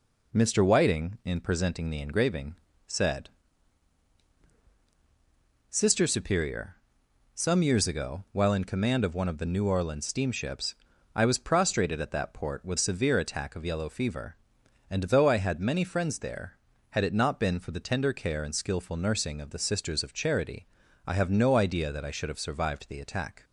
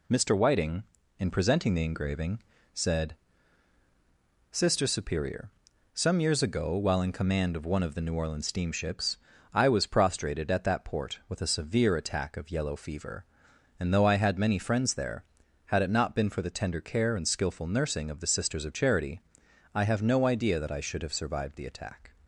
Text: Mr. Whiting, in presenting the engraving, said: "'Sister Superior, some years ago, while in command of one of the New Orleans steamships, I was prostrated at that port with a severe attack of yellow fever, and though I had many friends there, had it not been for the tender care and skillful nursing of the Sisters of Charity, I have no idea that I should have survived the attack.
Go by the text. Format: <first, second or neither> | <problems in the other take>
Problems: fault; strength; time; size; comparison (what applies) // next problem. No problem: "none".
second | skips "a"; at 12.7 s